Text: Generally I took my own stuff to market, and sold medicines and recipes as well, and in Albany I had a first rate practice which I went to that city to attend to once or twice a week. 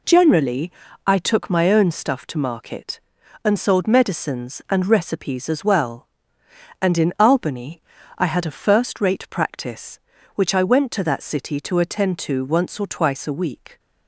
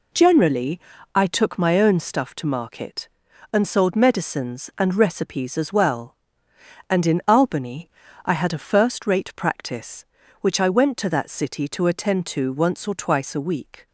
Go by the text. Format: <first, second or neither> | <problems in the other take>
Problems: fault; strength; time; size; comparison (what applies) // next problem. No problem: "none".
neither | pauses between "Generally" and "I"; slight; the same in both // pauses between "Albany" and "I"; the same in both